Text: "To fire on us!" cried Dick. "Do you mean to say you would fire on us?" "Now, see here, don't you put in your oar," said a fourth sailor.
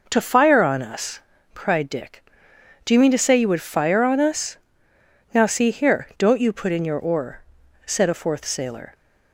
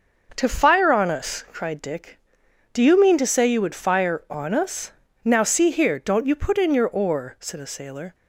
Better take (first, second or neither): first